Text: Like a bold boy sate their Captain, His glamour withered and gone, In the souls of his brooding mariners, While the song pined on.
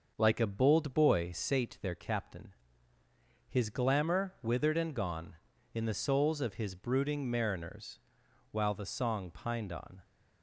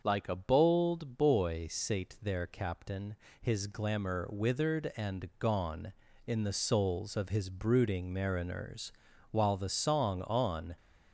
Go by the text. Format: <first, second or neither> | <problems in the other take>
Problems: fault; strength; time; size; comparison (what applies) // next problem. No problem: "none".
first | starts louder than the rest; until 1.0 s; 6.5 dB; noticeable in the first // skips "pined"; at 10.2 s